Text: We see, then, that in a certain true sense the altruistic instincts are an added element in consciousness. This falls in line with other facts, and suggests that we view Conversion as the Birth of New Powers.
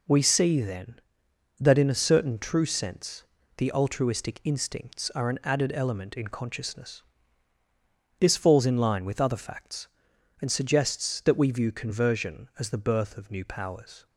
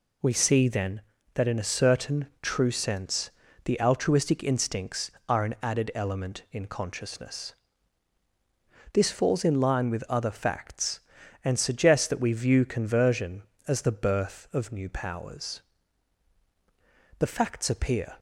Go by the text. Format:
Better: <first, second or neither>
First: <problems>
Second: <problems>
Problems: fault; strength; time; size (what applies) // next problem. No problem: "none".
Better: first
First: pauses between "sense" and "the"; slight; at 3.2 s; 0.34 s long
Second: pauses between "sense" and "the"; slight; at 3.3 s; 0.34 s long // goes on to say "The facts appear"; noticeable; from 17.1 s on; 0.98 s long